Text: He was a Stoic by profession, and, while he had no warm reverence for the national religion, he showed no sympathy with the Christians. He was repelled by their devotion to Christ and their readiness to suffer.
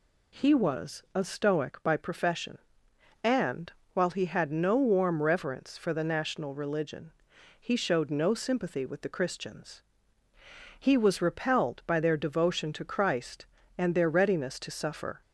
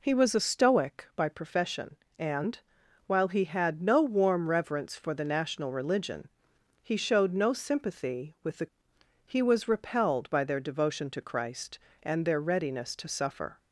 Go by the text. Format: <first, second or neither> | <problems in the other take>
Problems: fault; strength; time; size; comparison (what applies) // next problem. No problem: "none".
first | skips "Christians"; at 8.9 s